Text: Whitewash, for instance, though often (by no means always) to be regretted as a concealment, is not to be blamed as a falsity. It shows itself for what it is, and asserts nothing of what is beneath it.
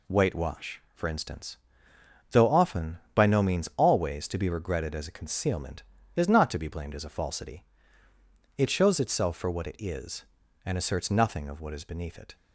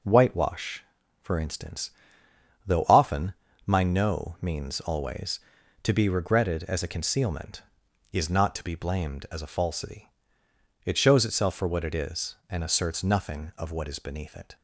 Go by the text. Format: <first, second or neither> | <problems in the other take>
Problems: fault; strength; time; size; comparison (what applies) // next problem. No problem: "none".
first | says "my" for "by"; at 3.6 s